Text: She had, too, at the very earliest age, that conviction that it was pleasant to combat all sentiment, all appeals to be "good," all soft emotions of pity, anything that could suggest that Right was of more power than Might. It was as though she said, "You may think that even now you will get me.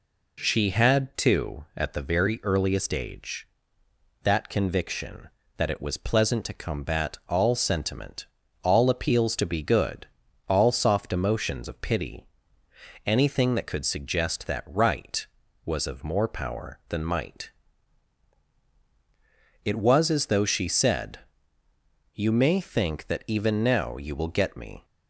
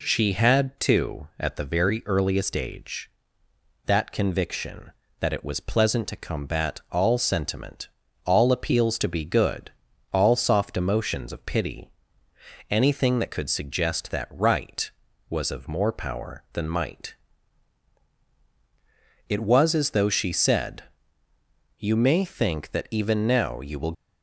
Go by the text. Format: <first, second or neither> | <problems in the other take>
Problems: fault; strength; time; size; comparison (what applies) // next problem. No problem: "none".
first | stops before "get me"; at 23.9 s